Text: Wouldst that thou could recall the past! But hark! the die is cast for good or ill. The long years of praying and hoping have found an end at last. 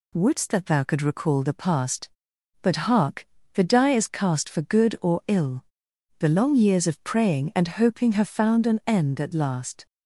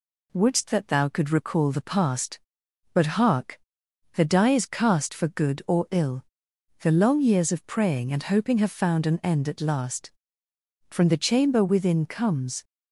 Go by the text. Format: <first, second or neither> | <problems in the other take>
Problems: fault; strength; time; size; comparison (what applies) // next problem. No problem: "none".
first | goes on to say "From the chamber within comes"; strong; from 10.9 s on; 1.7 s long